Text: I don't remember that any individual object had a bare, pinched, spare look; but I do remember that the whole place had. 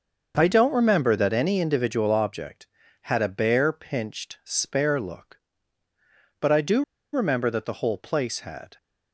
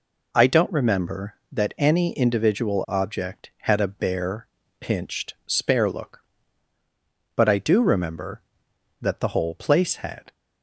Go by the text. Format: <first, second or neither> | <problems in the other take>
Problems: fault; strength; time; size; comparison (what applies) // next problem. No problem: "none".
second | starts louder than the rest; until 1.3 s; 6.5 dB // pauses between "do" and "remember"; slight; at 6.8 s; 0.31 s long